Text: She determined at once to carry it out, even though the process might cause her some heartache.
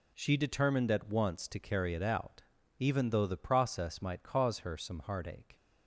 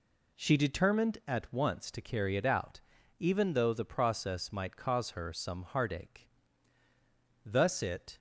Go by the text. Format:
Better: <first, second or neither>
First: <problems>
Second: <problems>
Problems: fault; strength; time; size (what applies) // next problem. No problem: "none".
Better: first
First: none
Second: goes on to say "Thus it"; noticeable; from 7.4 s on; 0.72 s long